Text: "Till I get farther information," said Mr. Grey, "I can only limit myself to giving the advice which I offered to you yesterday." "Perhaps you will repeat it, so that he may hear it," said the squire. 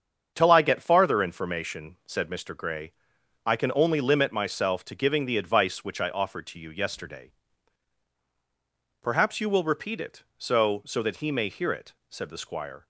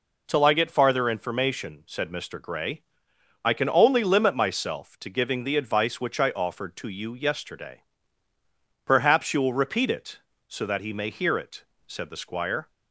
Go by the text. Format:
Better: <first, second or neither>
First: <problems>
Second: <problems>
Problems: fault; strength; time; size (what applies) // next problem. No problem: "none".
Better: second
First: starts louder than the rest; strong; until 1.3 s; 7 dB // says "so" twice; at 10.8 s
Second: none